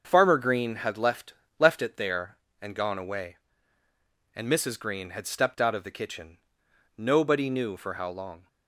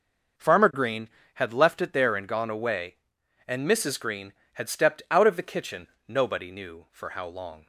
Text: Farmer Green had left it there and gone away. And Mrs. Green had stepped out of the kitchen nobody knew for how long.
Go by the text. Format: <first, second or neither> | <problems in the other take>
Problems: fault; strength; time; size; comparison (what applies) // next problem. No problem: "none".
second | starts louder than the rest; until 1.0 s; 6.5 dB; noticeable in the second // says "left" twice; at 1.5 s // pauses between "kitchen" and "nobody"; noticeable; at 6.3 s; 0.58 s long; slight in the second